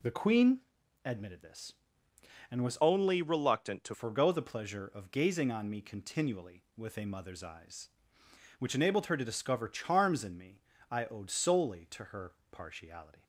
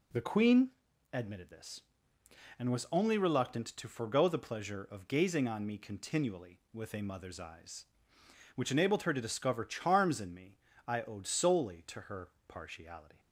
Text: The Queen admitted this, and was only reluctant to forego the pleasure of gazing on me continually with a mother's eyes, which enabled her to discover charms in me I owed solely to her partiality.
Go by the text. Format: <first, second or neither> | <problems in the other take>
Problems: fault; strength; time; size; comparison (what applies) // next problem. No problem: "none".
second | pauses between "Queen" and "admitted"; noticeable; at 0.5 s; 0.46 s long; also in the second // changes voice from "only" to "to"; from 2.8 to 3.9 s; 1.1 s long // pauses between "me" and "I"; slight; at 10.6 s; 0.30 s long; slight in the second // pauses between "her" and "partiality"; slight; at 12.3 s; 0.18 s long; slight in the second